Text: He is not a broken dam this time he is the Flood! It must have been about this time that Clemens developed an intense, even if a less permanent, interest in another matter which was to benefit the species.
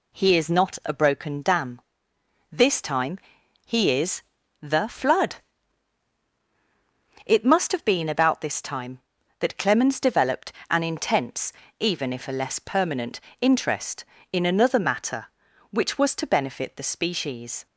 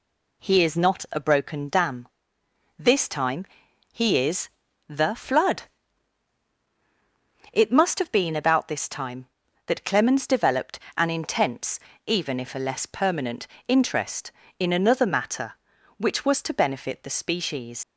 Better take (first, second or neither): first